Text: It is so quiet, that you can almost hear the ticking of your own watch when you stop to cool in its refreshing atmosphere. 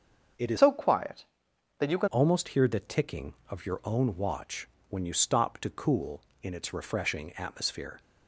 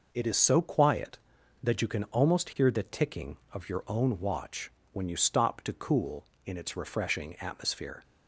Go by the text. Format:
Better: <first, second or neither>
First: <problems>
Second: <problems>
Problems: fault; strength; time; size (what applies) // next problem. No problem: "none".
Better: second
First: starts louder than the rest; until 1.8 s; 6.5 dB // changes voice from "so" to "can"; from 0.5 to 2.0 s; 1.5 s long // pauses between "watch" and "when"; slight; at 4.6 s; 0.22 s long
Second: pauses between "watch" and "when"; slight; at 4.6 s; 0.22 s long